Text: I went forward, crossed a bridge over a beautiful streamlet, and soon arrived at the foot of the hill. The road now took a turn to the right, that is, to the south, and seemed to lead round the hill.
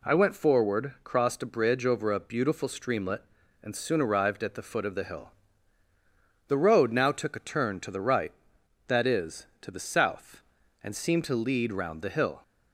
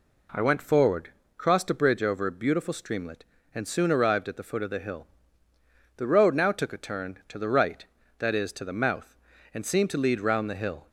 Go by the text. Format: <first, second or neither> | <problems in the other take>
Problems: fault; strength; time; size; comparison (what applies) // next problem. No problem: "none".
first | says "mouth" for "south"; at 8.7 s